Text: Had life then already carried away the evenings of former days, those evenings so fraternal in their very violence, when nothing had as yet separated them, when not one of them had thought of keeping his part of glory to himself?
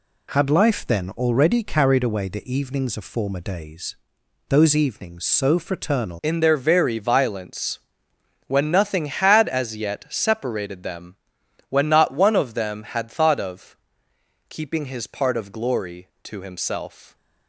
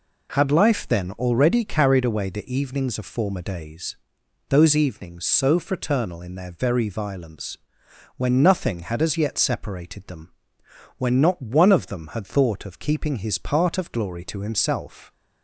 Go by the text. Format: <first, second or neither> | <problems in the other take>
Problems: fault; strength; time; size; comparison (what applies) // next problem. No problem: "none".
second | changes voice at "in"; from 6.2 s on; 10.9 s long // pauses between "of" and "keeping"; noticeable; at 13.7 s; 0.72 s long